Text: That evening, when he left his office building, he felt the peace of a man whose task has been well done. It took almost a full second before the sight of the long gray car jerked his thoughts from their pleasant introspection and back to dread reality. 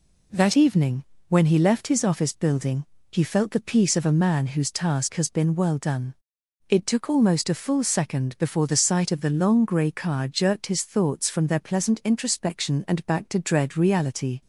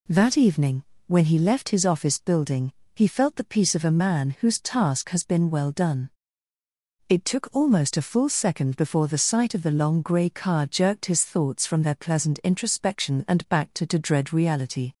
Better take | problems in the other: first | says "to" twice; at 13.8 s

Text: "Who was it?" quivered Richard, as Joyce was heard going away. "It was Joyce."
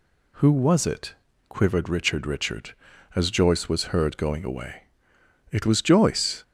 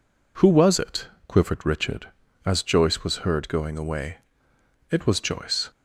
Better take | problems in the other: second | says "Richard" twice; at 2.2 s

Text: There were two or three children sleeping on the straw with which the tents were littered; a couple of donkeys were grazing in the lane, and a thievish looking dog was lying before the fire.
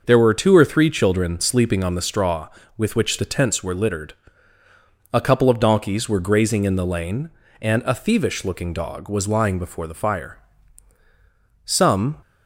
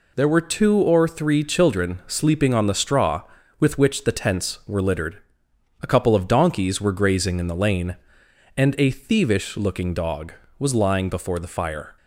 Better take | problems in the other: second | goes on to say "Some"; from 11.6 s on; 0.54 s long

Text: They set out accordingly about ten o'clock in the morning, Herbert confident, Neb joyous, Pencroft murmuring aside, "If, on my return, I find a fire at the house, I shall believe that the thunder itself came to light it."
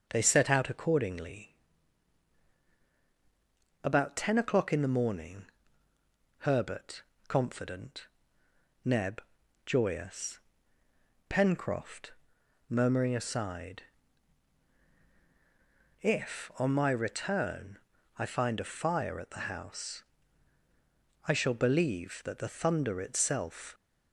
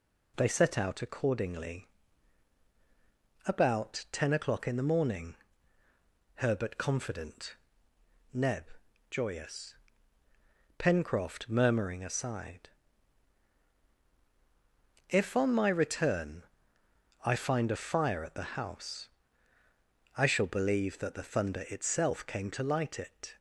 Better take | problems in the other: second | starts louder than the rest; until 1.0 s; 6.5 dB // pauses between "accordingly" and "about"; strong; at 1.5 s; 2.3 s long; strong in the second // pauses between "Herbert" and "confident"; slight; at 7.0 s; 0.24 s long // pauses between "Neb" and "joyous"; at 9.2 s; 0.44 s long; noticeable in the second // pauses between "Pencroft" and "murmuring"; noticeable; at 12.1 s; 0.56 s long // stops before "came to light it"; at 23.7 s

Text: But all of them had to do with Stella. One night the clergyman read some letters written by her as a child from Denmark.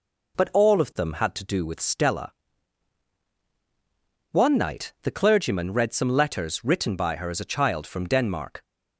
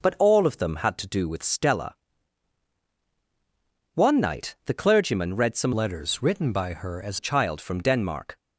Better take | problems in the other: first | changes voice from "letters" to "as"; from 5.7 to 7.1 s; 1.4 s long

